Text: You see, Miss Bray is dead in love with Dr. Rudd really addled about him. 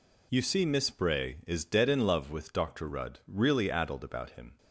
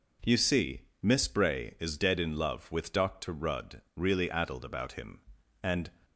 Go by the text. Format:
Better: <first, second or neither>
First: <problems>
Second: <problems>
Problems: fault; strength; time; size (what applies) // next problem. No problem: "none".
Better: first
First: none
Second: pauses between "Rudd" and "really"; slight; at 3.8 s; 0.16 s long // goes on to say "And"; slight; from 5.6 s on; 0.26 s long